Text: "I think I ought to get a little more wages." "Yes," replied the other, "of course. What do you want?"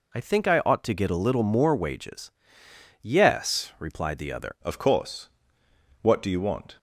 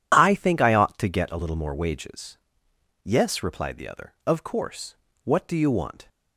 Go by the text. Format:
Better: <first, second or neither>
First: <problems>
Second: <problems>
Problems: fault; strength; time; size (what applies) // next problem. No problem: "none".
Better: second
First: changes voice at "of"; from 4.6 s on; 2.1 s long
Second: none